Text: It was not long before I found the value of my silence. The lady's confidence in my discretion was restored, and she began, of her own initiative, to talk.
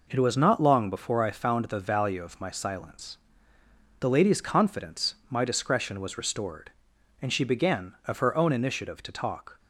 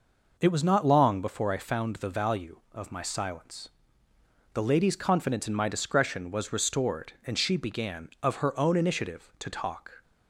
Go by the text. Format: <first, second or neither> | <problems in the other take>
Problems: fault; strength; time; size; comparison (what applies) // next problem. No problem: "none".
second | skips "in"; at 5.2 s